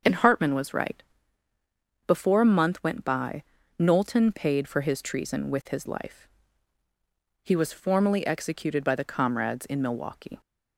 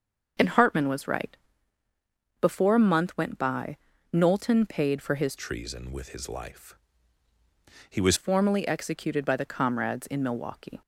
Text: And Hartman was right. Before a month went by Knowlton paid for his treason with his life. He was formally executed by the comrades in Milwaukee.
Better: first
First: starts louder than the rest; until 2.1 s; 6.5 dB // pauses between "by" and "Knowlton"; slight; at 3.4 s; 0.36 s long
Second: starts louder than the rest; until 2.4 s; 6.5 dB // pauses between "by" and "Knowlton"; slight; at 3.7 s; 0.36 s long // changes voice from "treason" to "was"; from 5.3 to 8.1 s; 2.8 s long

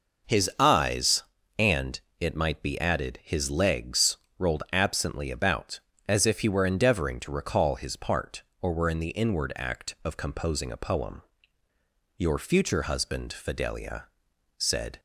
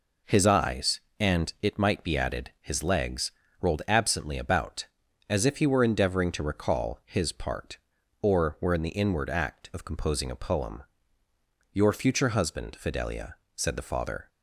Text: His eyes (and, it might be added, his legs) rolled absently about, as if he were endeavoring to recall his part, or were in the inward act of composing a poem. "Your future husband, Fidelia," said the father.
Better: second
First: stops before "the father"; at 14.9 s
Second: none

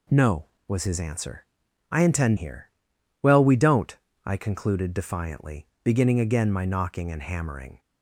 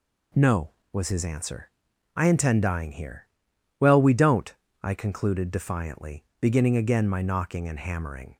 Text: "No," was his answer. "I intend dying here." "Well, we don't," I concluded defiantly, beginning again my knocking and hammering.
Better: second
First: skips "dying"; at 2.3 s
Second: none

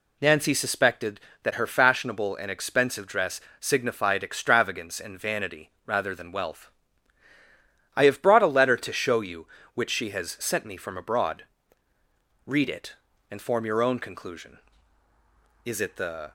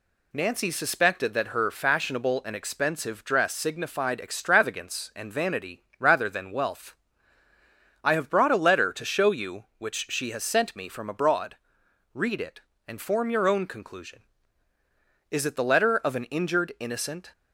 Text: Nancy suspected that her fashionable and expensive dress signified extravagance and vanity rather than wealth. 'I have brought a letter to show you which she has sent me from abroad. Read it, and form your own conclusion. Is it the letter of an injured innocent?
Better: second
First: pauses between "dress" and "signified"; slight; at 3.4 s; 0.20 s long // pauses between "vanity" and "rather"; slight; at 5.7 s; 0.16 s long // stops before "letter of an injured innocent"; at 16.2 s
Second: pauses between "vanity" and "rather"; slight; at 5.8 s; 0.16 s long

